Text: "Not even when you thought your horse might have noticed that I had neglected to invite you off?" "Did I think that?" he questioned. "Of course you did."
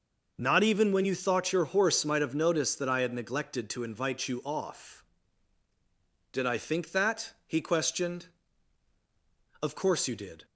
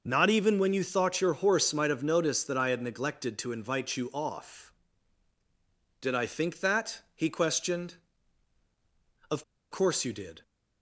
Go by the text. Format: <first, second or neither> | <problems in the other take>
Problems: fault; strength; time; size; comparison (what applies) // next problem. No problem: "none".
first | pauses between "Of" and "course"; slight; at 9.4 s; 0.28 s long